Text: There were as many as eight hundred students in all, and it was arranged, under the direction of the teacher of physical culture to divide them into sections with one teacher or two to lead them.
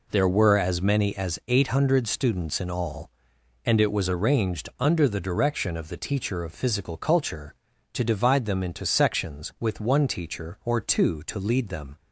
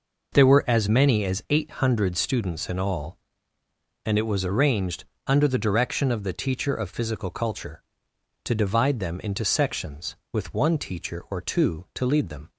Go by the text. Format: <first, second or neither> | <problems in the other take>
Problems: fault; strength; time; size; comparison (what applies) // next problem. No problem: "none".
neither | none